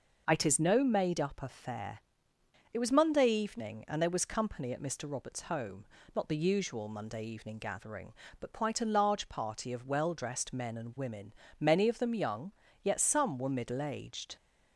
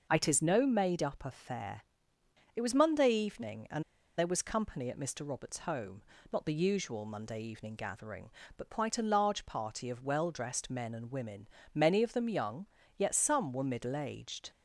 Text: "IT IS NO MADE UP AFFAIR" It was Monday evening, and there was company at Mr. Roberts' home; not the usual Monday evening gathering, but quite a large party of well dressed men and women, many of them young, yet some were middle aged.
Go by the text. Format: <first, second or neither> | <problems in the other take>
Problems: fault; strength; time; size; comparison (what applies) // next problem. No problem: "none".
first | pauses between "AFFAIR" and "It"; noticeable; at 1.8 s; 0.74 s long; noticeable in the first // pauses between "and" and "there"; slight; at 3.8 s; 0.35 s long